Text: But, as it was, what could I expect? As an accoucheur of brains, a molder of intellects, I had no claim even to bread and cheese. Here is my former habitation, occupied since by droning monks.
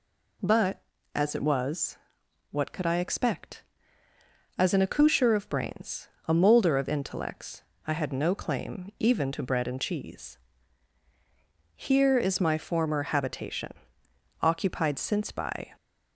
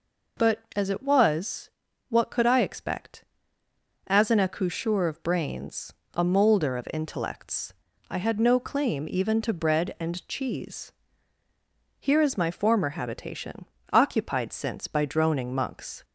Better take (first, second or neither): second